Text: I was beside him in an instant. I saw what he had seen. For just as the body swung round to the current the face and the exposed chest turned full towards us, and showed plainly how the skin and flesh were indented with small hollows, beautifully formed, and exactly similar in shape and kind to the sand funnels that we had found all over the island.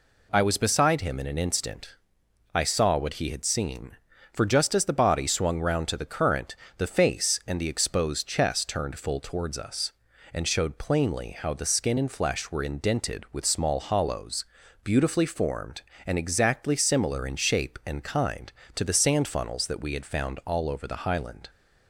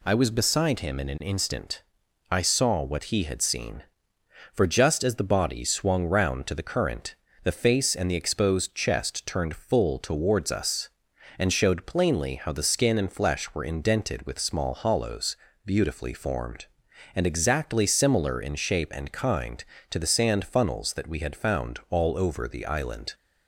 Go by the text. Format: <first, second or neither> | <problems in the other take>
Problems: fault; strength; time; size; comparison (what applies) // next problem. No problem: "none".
second | pauses between "current" and "the"; slight; at 6.5 s; 0.21 s long; slight in the second // says "highland" for "island"; at 21.0 s